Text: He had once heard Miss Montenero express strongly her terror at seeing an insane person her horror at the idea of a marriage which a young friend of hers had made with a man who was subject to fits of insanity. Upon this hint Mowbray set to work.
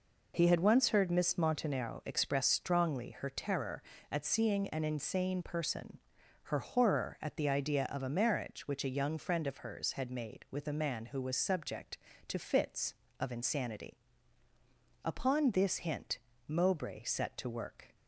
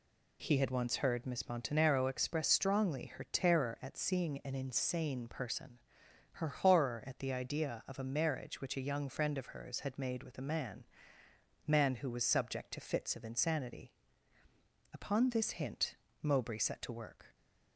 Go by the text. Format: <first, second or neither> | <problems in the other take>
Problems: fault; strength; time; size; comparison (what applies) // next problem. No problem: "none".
first | pauses between "person" and "her"; noticeable; at 5.7 s; 0.54 s long; noticeable in the first // says "man" twice; at 11.6 s // pauses between "hint" and "Mowbray"; slight; at 15.9 s; 0.28 s long; slight in the first